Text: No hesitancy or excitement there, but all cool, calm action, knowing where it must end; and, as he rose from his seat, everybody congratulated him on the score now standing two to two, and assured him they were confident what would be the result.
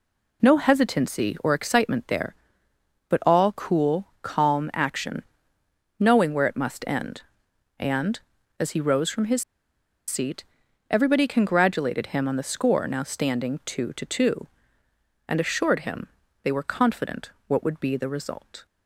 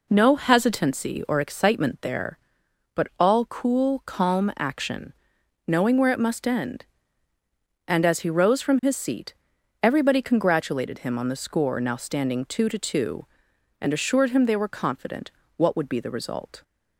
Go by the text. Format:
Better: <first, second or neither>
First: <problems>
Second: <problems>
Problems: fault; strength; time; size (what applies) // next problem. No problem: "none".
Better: second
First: pauses between "his" and "seat"; noticeable; at 9.4 s; 0.64 s long // pauses between "him" and "they"; slight; at 16.0 s; 0.34 s long // pauses between "confident" and "what"; slight; at 17.2 s; 0.18 s long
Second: pauses between "confident" and "what"; slight; at 15.3 s; 0.26 s long